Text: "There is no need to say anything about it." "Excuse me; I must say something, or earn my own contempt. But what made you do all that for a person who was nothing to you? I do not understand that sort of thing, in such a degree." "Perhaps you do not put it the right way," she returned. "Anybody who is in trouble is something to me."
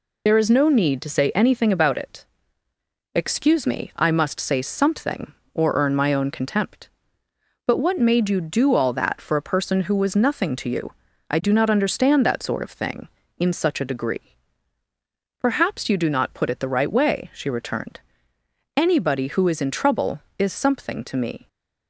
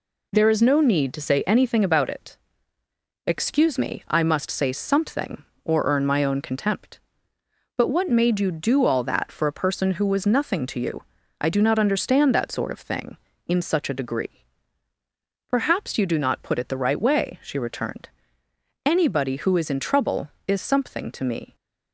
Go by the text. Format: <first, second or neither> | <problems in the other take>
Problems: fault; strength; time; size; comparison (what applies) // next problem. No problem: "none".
second | loses the start of "There"; at 0.2 s; 60 ms